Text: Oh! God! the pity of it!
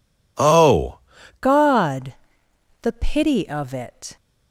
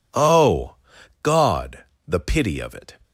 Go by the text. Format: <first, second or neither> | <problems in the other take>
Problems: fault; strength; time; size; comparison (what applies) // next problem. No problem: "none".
second | changes voice at "God"; from 1.4 s on; 2.7 s long